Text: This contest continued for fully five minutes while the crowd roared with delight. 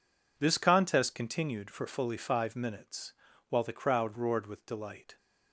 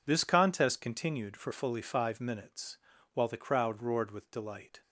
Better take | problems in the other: neither | pauses between "minutes" and "while"; slight; the same in both

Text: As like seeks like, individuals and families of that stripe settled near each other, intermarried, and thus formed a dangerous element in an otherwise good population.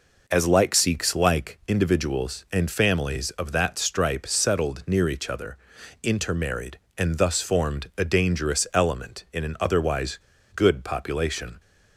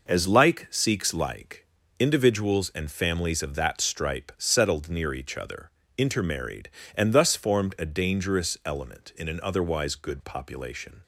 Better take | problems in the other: second | pauses between "otherwise" and "good"; at 10.1 s; 0.37 s long

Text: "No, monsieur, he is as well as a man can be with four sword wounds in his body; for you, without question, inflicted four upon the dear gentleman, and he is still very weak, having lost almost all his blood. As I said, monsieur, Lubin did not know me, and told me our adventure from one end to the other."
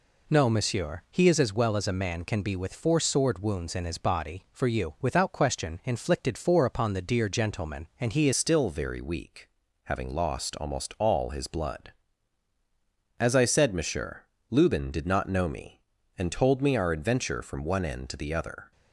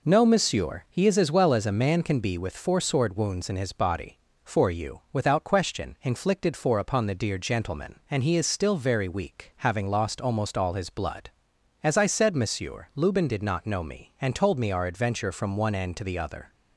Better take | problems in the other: second | changes voice at "still"; from 8.3 s on; 10.4 s long

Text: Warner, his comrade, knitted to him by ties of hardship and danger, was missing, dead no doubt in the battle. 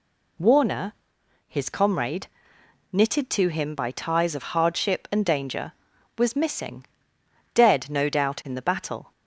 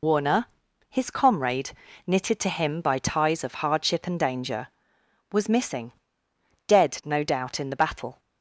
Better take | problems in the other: first | loses the start of "Warner"; at 0.0 s; 75 ms

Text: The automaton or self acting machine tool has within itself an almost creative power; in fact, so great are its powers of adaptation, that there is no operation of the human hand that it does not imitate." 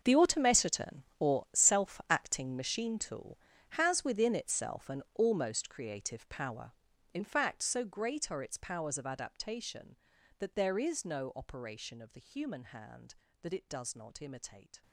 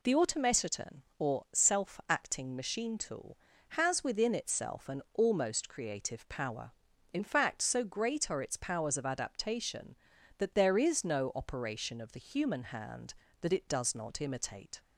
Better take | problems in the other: second | gets quieter; strong; throughout; 16.5 dB

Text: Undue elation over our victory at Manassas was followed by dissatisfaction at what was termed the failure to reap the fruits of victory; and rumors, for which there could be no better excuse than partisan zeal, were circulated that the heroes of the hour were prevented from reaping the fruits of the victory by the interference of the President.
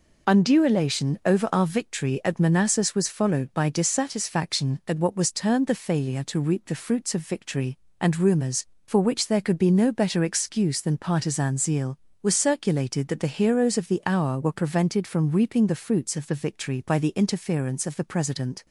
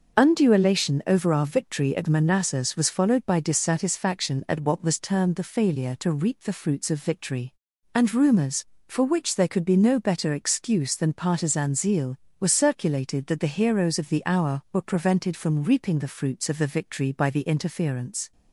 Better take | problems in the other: first | starts louder than the rest; until 1.2 s; 6.5 dB // stops before "of the President"; at 18.3 s

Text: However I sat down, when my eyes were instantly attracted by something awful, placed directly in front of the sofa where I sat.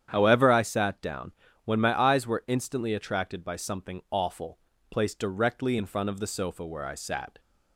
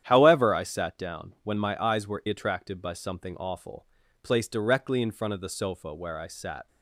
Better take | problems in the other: first | starts louder than the rest; strong; until 1.0 s; 10 dB; strong in the first // skips "instantly"; at 2.2 s

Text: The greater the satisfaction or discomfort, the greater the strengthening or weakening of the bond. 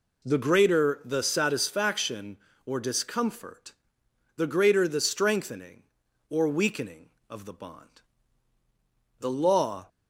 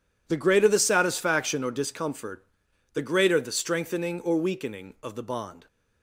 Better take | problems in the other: second | goes on to say "The Law"; noticeable; from 9.1 s on; 0.68 s long

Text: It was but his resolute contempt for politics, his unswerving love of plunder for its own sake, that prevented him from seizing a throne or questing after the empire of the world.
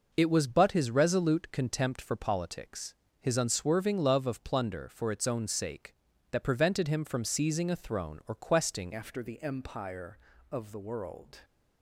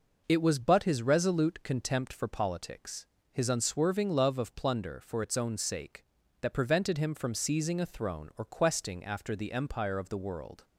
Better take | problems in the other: second | changes voice at "after"; from 8.9 s on; 2.4 s long

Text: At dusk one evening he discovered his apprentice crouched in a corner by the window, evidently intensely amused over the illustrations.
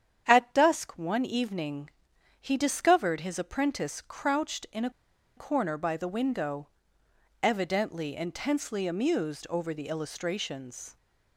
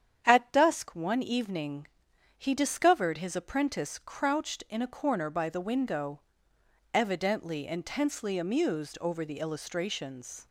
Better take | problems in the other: second | starts louder than the rest; strong; until 1.2 s; 8.5 dB; strong in the second // pauses between "evening" and "he"; noticeable; at 1.8 s; 0.50 s long; noticeable in the second // pauses between "a" and "corner"; noticeable; at 4.8 s; 0.47 s long

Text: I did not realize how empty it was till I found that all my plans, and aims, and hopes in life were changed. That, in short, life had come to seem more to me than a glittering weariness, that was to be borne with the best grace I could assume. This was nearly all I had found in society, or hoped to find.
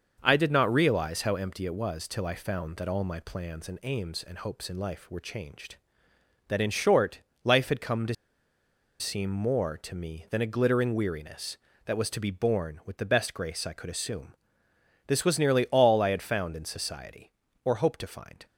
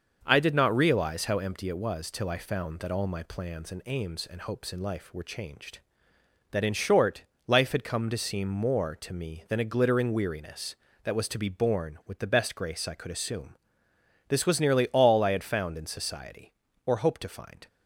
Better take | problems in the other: second | starts louder than the rest; until 1.2 s; 6 dB; also in the second // pauses between "to" and "seem"; noticeable; at 8.1 s; 0.85 s long

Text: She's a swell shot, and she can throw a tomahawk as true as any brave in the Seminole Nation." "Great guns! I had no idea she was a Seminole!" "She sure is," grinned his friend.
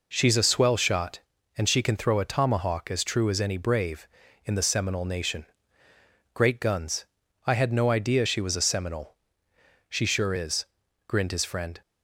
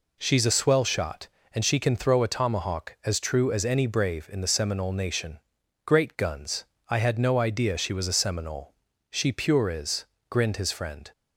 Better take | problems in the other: first | says "pure" for "sure"; at 9.3 s

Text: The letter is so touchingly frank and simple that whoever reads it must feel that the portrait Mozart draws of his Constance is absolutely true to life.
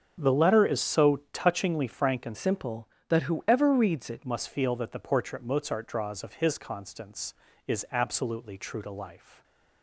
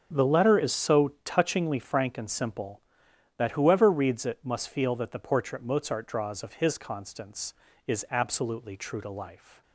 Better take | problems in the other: second | starts louder than the rest; until 1.2 s; 6.5 dB; also in the second // changes voice from "simple" to "it"; from 2.3 to 4.2 s; 1.9 s long

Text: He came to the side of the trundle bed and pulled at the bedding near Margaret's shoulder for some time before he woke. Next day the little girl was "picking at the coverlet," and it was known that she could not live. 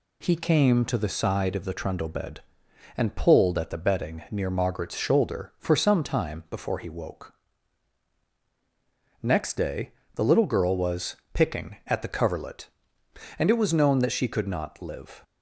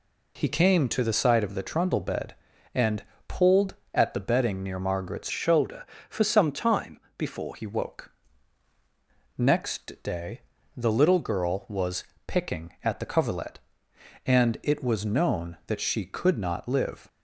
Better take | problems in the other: first | pauses between "and" and "pulled"; slight; at 3.0 s; 0.24 s long // changes voice from "shoulder" to "before"; from 5.3 to 7.5 s; 2.2 s long // pauses between "time" and "before"; slight; at 7.0 s; 0.16 s long // pauses between "day" and "the"; slight; at 10.4 s; 0.34 s long; slight in the first // pauses between "was" and "picking"; slight; at 12.0 s; 0.24 s long; slight in the first

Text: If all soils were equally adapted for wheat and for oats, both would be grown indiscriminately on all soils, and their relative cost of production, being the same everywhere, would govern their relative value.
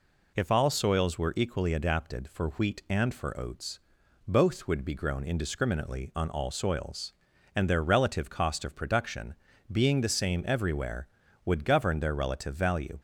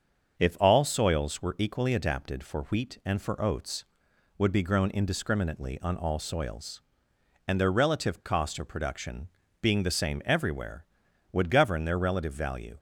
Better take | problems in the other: first | starts louder than the rest; until 1.4 s; 6.5 dB // skips "both"; at 4.1 s

